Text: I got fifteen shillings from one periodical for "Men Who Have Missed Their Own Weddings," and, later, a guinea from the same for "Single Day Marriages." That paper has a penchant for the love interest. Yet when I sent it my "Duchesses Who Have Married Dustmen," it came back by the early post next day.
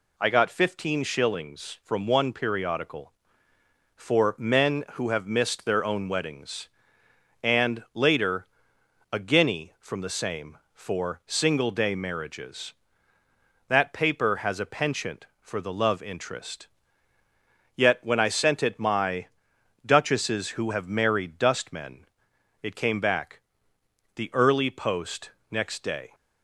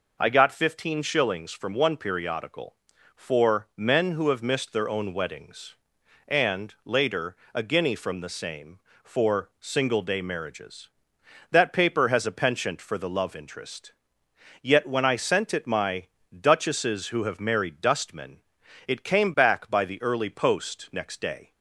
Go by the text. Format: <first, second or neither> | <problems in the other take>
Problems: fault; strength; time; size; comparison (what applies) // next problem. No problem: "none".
second | pauses between "my" and "Duchesses"; noticeable; at 19.2 s; 0.58 s long; slight in the second // skips "by"; at 23.7 s // pauses between "post" and "next"; slight; at 25.3 s; 0.20 s long